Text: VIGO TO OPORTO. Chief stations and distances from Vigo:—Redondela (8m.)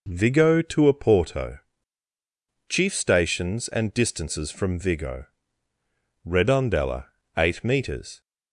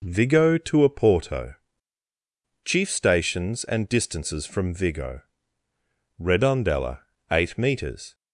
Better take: neither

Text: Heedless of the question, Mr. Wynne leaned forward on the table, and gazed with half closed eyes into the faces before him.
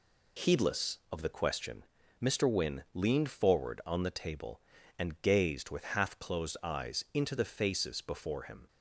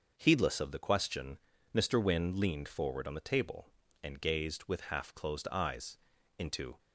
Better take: first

